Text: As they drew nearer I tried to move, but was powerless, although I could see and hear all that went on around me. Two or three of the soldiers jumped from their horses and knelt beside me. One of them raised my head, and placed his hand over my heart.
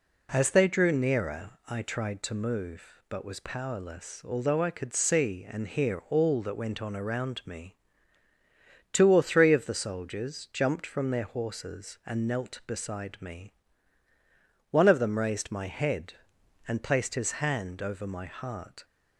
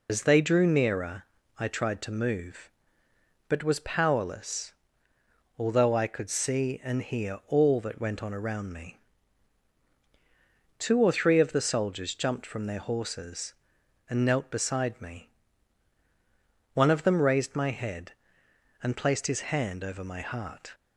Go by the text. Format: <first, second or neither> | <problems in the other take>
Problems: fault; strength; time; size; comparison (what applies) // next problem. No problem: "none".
first | loses the start of "As"; at 0.0 s; 65 ms // pauses between "nearer" and "I"; slight; at 1.2 s; 0.34 s long